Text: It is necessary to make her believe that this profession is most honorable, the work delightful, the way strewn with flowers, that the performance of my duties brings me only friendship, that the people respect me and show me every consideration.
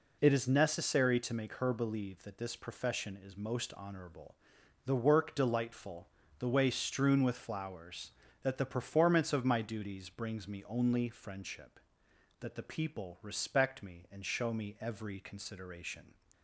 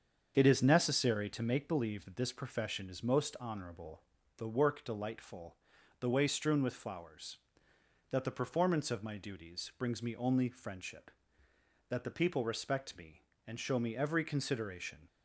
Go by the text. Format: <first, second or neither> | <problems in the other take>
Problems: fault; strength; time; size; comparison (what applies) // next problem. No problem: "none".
first | starts louder than the rest; until 1.3 s; 7 dB // skips "her"; at 1.6 s